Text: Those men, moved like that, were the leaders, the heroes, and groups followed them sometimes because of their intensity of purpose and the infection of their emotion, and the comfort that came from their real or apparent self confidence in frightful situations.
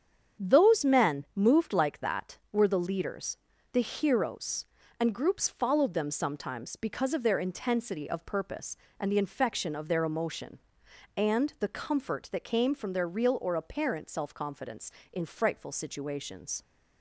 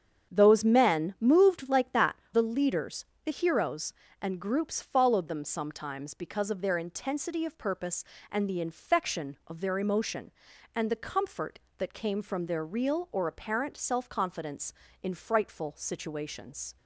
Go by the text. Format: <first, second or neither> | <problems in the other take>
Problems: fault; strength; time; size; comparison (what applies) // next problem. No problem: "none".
first | starts louder than the rest; strong; until 1.3 s; 8 dB; strong in the first // skips "were"; at 2.2 s